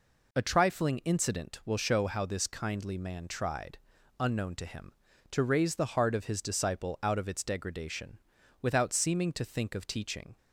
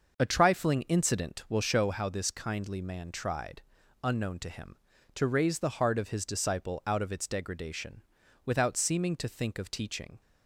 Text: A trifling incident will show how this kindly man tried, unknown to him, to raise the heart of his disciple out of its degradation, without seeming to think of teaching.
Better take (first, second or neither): first